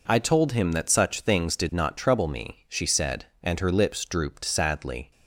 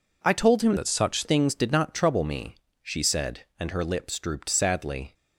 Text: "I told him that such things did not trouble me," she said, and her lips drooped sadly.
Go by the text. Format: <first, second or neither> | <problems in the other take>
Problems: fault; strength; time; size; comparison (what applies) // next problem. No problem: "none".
first | changes voice from "that" to "such"; from 0.7 to 1.2 s; 0.5 s long